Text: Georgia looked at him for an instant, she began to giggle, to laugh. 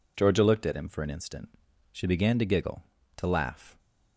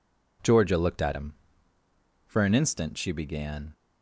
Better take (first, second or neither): first